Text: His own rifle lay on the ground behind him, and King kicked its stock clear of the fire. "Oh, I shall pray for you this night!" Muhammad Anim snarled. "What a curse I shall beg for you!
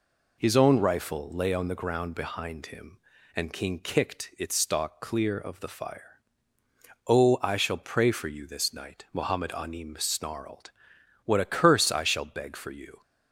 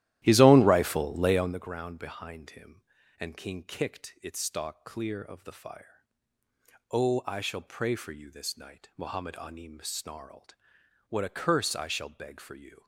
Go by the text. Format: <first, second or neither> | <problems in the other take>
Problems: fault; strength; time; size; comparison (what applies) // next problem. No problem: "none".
first | starts louder than the rest; strong; until 1.6 s; 14 dB